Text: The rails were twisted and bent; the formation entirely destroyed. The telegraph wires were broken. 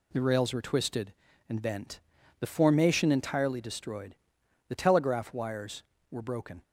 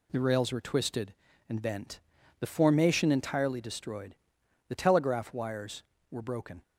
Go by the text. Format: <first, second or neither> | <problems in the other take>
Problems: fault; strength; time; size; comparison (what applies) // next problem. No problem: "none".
neither | none